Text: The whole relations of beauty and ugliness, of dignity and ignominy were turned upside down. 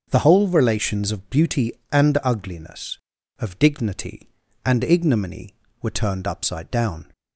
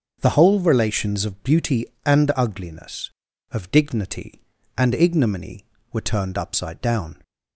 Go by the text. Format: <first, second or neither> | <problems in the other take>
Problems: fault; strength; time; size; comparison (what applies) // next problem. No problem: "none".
neither | starts louder than the rest; the same in both